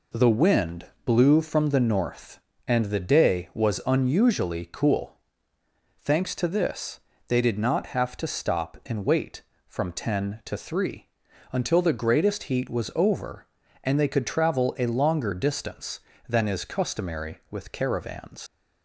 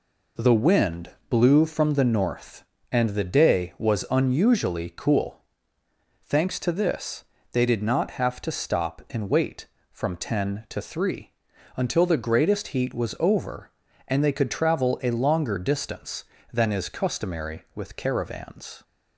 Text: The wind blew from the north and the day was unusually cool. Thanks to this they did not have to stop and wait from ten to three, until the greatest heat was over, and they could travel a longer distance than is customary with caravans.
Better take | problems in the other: second | pauses between "wind" and "blew"; slight; at 0.8 s; 0.22 s long; slight in the second // pauses between "this" and "they"; slight; at 7.0 s; 0.28 s long; slight in the second // leaves "caravans" unfinished; at 18.4 s; 120 ms

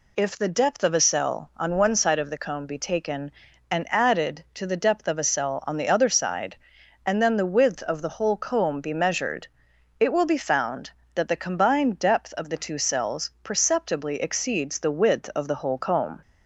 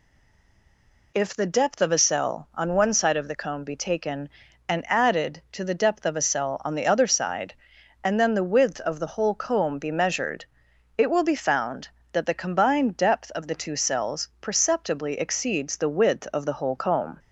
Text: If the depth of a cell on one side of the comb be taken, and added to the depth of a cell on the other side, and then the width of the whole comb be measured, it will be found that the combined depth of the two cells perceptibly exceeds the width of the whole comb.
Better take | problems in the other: first | stays silent before the first word; until 1.1 s; 1.1 s long

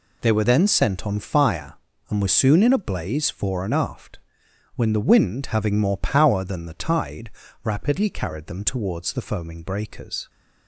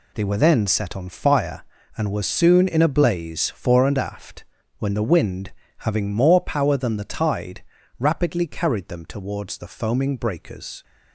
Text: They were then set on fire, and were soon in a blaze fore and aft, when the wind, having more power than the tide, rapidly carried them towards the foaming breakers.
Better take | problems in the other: second | says "sent" for "set"; at 0.6 s

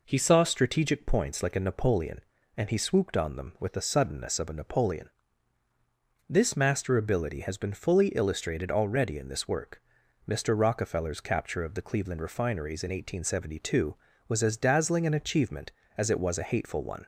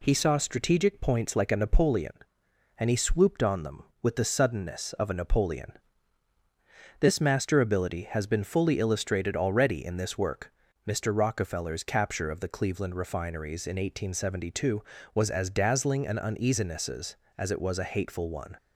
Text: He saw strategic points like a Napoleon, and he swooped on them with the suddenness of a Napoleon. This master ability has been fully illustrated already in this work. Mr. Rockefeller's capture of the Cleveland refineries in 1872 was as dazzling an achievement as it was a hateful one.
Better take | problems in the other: first | says "uneasinesses" for "achievement"; at 16.1 s

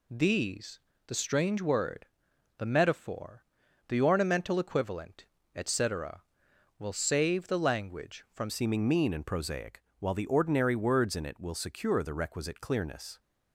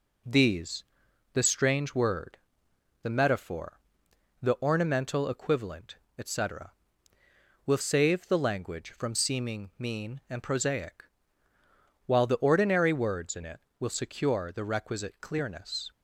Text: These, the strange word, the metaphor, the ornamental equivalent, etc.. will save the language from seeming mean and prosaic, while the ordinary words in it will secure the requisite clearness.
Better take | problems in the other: second | changes voice at "seeming"; from 8.4 s on; 4.7 s long

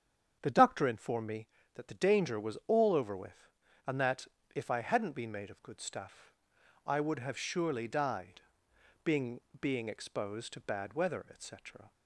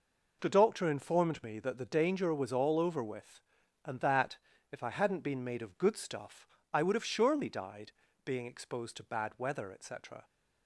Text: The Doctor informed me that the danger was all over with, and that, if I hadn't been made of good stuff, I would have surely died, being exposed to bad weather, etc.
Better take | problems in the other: second | starts louder than the rest; strong; until 1.4 s; 8 dB // says "being" twice; at 9.5 s

